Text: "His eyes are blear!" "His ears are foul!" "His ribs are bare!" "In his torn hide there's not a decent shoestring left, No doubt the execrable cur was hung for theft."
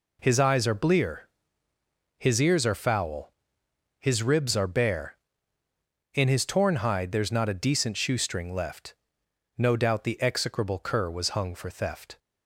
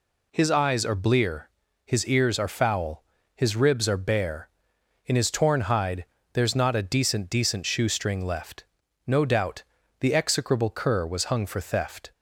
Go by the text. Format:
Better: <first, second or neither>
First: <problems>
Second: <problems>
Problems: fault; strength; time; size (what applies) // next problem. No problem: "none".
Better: first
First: none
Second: pauses between "hide" and "there's"; slight; at 6.0 s; 0.30 s long // says "decent" twice; at 7.2 s // pauses between "doubt" and "the"; slight; at 9.6 s; 0.36 s long